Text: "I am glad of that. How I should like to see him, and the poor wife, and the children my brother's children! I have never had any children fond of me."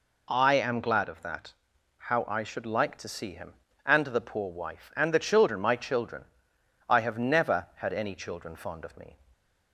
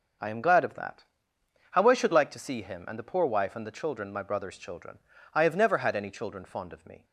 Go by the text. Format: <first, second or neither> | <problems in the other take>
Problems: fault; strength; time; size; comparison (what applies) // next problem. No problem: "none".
second | skips "brother's"; at 5.7 s